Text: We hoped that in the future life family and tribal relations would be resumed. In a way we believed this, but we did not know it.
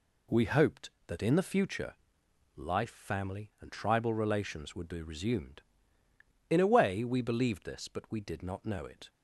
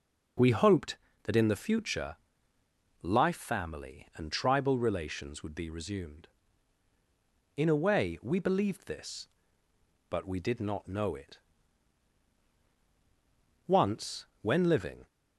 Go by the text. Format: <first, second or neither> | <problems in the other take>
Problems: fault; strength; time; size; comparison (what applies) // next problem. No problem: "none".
first | pauses between "future" and "life"; noticeable; at 2.1 s; 0.88 s long; noticeable in the first // goes on to say "Once when living"; from 13.6 s on; 1.4 s long